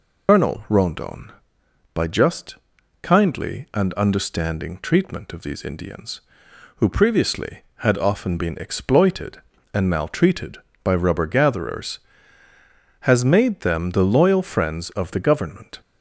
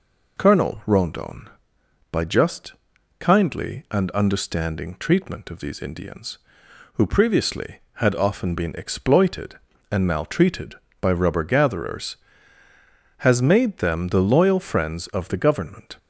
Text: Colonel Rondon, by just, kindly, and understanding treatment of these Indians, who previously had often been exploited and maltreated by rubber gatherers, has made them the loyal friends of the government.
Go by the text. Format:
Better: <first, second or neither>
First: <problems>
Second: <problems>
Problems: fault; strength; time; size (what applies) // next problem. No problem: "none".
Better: second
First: loses the start of "Colonel"; at 0.2 s; 85 ms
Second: none